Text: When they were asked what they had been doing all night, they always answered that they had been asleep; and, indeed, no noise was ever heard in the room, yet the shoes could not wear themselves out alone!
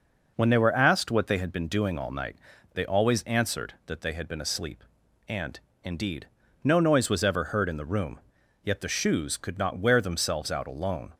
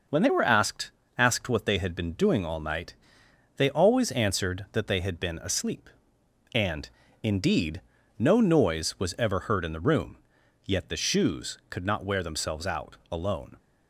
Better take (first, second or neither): first